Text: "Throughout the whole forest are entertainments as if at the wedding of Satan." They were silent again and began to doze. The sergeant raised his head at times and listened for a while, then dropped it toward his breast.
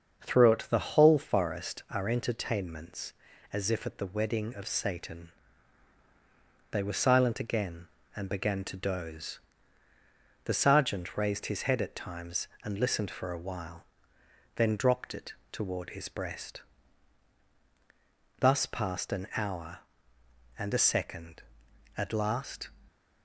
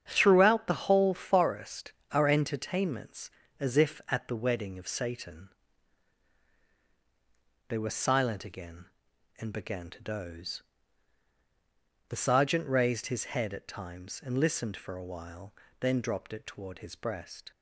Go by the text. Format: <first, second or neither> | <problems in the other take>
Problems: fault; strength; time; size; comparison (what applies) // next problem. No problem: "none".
second | starts louder than the rest; until 1.2 s; 6.5 dB; strong in the second // pauses between "it" and "toward"; slight; at 15.3 s; 0.18 s long // goes on to say "Thus passed an hour and a second at last"; strong; from 18.3 s on; 4.3 s long